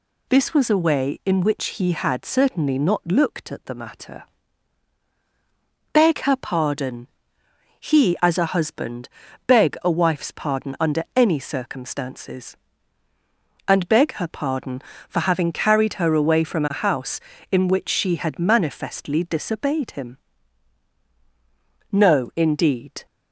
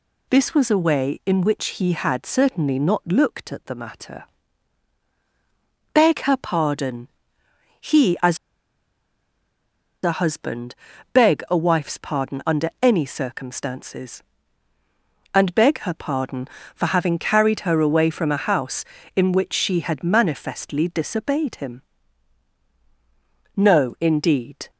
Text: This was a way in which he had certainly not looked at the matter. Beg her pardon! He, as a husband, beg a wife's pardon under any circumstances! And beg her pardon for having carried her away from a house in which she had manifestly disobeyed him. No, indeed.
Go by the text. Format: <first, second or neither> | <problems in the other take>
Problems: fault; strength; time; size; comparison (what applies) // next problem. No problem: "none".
first | pauses between "as" and "a"; strong; at 8.3 s; 1.6 s long